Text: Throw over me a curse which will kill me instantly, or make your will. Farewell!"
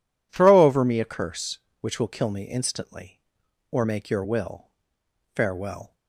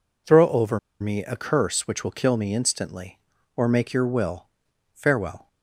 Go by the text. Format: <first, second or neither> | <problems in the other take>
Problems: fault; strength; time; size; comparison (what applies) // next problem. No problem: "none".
first | pauses between "over" and "me"; slight; at 0.7 s; 0.22 s long